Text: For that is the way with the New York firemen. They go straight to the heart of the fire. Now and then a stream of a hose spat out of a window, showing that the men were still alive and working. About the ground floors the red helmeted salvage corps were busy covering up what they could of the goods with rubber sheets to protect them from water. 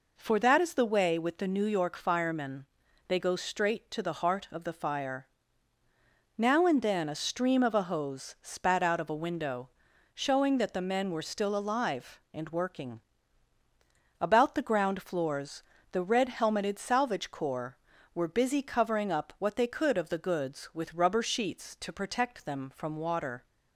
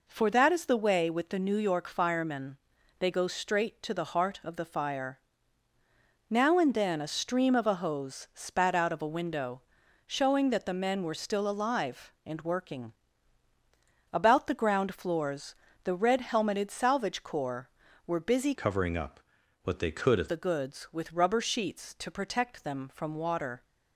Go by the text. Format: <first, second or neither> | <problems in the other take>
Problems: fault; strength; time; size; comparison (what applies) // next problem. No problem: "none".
first | pauses between "floors" and "the"; slight; at 15.5 s; 0.30 s long; slight in the first // changes voice from "covering" to "of"; from 18.5 to 20.2 s; 1.7 s long // pauses between "up" and "what"; noticeable; at 19.1 s; 0.46 s long